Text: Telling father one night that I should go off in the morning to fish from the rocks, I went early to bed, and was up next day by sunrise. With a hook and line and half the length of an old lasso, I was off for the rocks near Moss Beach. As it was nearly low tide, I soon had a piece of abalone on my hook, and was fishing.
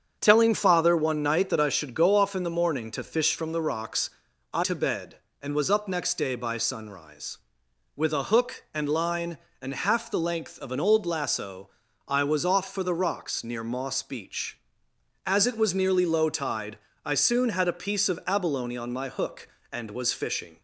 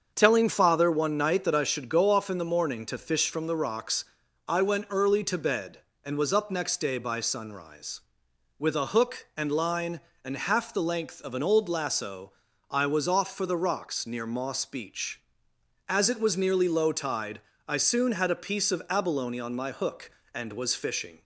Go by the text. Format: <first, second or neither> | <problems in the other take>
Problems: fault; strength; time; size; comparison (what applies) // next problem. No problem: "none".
second | starts louder than the rest; strong; until 1.2 s; 7.5 dB; also in the second // skips "went early"; at 4.6 s